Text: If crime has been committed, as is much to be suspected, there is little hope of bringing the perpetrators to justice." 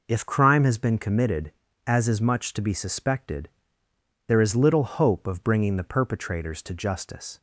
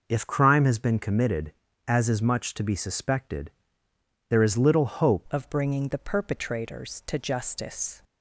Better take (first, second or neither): first